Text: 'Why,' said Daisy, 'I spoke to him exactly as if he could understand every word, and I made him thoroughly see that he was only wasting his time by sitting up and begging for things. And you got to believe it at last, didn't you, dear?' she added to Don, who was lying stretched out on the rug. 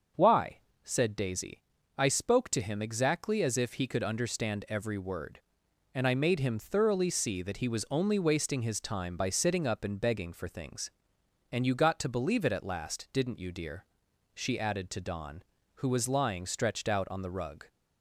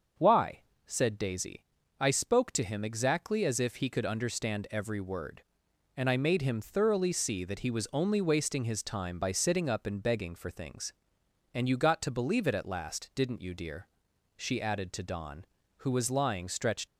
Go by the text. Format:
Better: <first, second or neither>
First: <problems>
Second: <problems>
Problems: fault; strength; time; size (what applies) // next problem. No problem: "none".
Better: first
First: starts louder than the rest; until 1.4 s; 6.5 dB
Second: starts louder than the rest; until 1.4 s; 6.5 dB // stops before "out on the rug"; at 16.8 s